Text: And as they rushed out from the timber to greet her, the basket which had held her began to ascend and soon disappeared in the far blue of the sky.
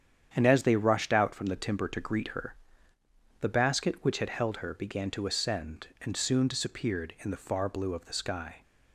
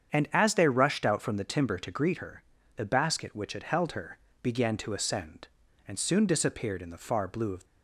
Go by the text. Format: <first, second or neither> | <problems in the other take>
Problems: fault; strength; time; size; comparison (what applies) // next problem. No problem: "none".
first | starts louder than the rest; strong; until 1.1 s; 8 dB; strong in the first // pauses between "her" and "began"; slight; at 4.1 s; 0.24 s long // stops before "the sky"; at 7.6 s